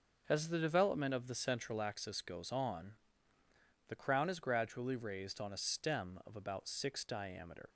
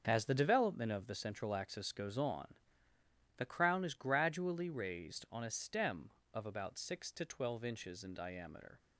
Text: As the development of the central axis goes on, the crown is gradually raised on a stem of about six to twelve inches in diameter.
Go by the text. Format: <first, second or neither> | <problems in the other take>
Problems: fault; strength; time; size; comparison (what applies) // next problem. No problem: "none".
second | starts louder than the rest; until 1.2 s; 6 dB; also in the second // skips "to twelve inches in"; at 7.0 s